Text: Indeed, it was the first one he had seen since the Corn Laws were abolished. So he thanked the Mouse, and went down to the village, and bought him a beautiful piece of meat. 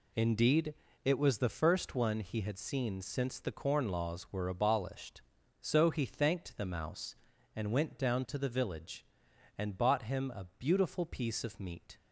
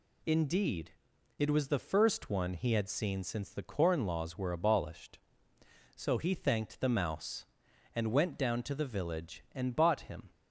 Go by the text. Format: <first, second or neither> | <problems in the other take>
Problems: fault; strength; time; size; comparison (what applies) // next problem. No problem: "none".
first | stops before "a beautiful piece of meat"; at 10.3 s